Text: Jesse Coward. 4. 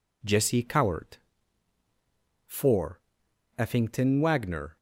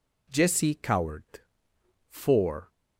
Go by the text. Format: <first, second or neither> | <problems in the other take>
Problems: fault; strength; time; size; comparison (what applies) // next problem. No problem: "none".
second | goes on to say "Effington Wagner"; noticeable; from 3.5 s on; 1.1 s long